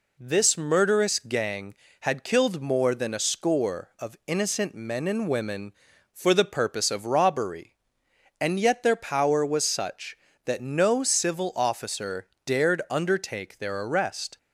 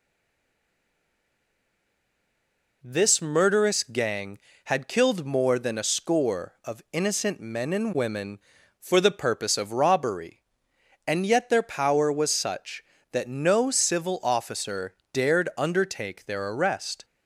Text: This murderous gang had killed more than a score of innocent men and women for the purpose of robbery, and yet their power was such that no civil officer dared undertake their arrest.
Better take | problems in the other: first | stays silent before the first word; strong; until 2.8 s; 2.8 s long // pauses between "officer" and "dared"; slight; at 14.9 s; 0.18 s long; slight in the first

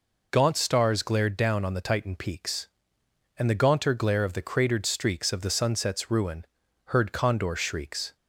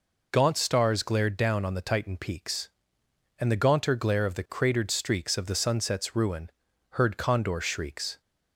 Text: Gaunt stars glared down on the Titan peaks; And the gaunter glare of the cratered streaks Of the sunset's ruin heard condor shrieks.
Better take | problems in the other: neither | pauses between "ruin" and "heard"; the same in both

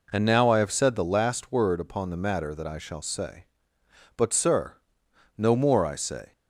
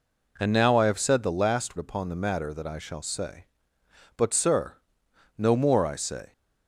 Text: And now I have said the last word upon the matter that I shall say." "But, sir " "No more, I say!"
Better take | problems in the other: first | skips "word"; at 1.7 s

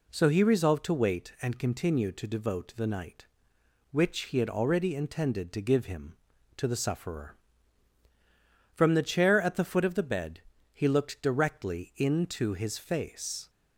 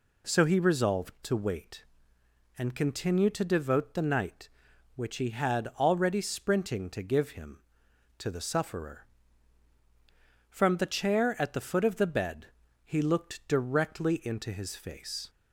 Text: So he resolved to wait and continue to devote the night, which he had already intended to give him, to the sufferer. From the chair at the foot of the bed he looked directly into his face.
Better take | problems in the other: first | says "sprinting" for "intended"; at 6.1 s // pauses between "bed" and "he"; slight; at 12.4 s; 0.36 s long; slight in the first

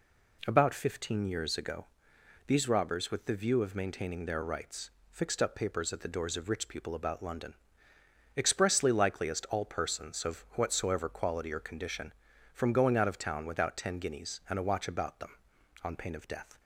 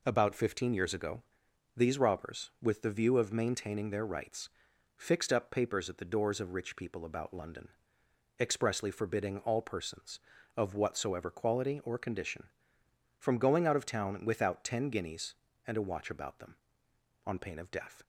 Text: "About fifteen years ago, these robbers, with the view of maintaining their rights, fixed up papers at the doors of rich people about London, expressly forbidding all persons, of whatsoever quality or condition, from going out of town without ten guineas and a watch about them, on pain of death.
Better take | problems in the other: second | says "likeliest" for "forbidding"; at 8.8 s

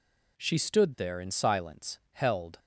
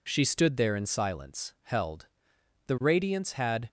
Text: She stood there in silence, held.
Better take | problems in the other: first | goes on to say "The radiance had"; noticeable; from 2.6 s on; 1.0 s long

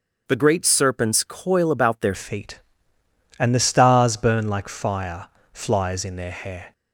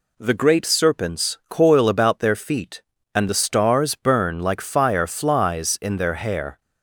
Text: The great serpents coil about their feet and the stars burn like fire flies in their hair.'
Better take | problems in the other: second | starts louder than the rest; until 1.2 s; 7 dB // changes voice at "feet"; from 2.1 s on; 4.6 s long // pauses between "fire" and "flies"; slight; at 5.2 s; 0.24 s long

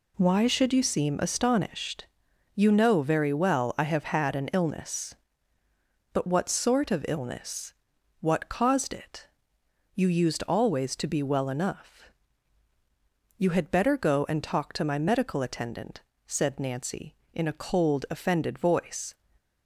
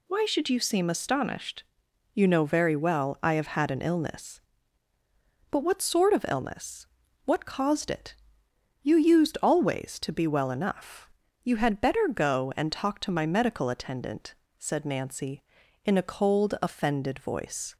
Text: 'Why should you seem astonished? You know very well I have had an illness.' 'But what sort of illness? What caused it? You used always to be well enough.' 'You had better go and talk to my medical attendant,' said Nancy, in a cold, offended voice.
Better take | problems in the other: neither | none

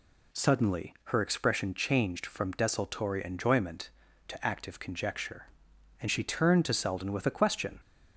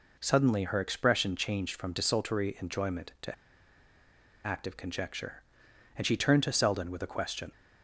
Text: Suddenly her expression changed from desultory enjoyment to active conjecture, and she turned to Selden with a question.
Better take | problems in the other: first | pauses between "to" and "active"; at 3.3 s; 1.1 s long

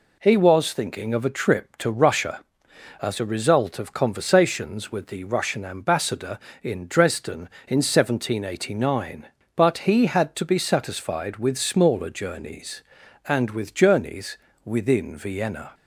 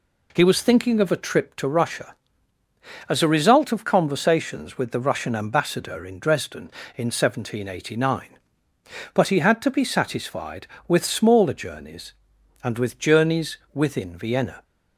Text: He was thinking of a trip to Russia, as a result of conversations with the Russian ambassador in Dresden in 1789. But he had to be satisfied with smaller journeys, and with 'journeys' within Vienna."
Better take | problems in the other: neither | pauses between "journeys" and "within"; slight; the same in both

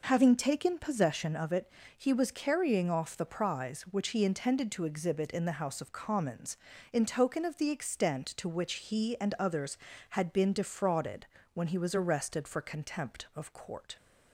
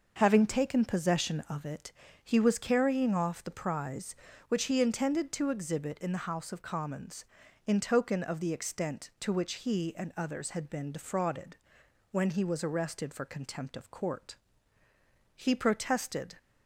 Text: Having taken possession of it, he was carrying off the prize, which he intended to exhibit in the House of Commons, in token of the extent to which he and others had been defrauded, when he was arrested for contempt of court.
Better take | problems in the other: first | goes on to say "He protested"; noticeable; from 15.3 s on; 1.0 s long

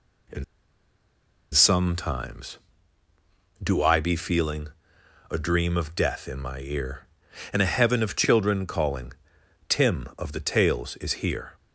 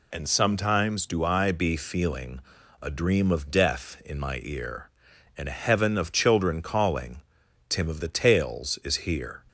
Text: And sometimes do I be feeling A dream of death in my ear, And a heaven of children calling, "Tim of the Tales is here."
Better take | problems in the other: second | pauses between "And" and "sometimes"; at 0.4 s; 1.0 s long // pauses between "feeling" and "A"; noticeable; at 4.6 s; 0.60 s long; also in the second

